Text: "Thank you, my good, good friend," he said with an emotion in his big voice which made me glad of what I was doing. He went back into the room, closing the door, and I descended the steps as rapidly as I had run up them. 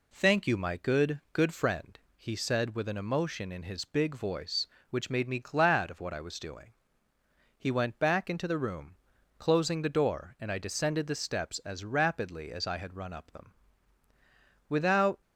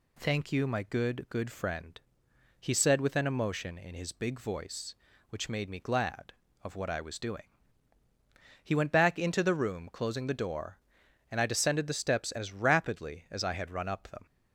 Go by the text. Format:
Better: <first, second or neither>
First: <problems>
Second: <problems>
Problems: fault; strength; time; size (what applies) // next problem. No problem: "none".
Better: second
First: goes on to say "Without"; from 14.6 s on; 0.54 s long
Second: none